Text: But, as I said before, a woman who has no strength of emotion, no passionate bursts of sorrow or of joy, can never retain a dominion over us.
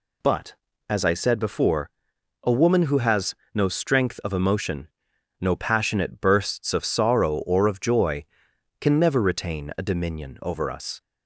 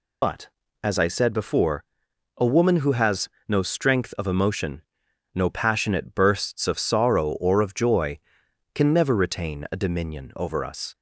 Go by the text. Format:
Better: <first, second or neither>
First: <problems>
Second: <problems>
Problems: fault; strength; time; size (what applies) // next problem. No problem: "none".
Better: first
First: pauses between "has" and "no"; slight; at 3.3 s; 0.18 s long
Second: loses the start of "But"; at 0.2 s; 60 ms // pauses between "has" and "no"; slight; at 3.2 s; 0.18 s long